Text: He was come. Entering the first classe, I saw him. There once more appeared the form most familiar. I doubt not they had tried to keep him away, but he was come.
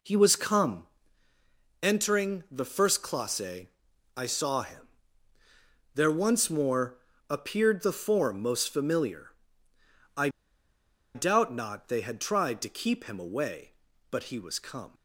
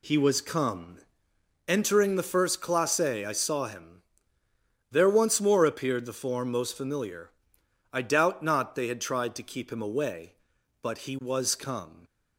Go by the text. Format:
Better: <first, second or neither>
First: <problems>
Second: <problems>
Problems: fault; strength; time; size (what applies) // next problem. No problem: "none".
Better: second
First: pauses between "more" and "appeared"; slight; at 6.9 s; 0.32 s long // pauses between "I" and "doubt"; noticeable; at 10.2 s; 0.86 s long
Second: none